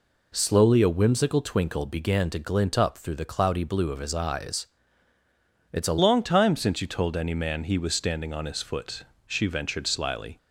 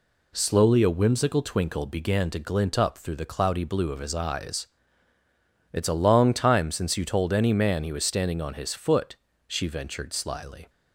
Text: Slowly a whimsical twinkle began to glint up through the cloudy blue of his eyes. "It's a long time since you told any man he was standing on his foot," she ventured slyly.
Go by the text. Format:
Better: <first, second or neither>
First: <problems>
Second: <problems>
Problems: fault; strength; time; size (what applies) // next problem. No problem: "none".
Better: second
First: changes voice at "long"; from 5.9 s on; 4.4 s long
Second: none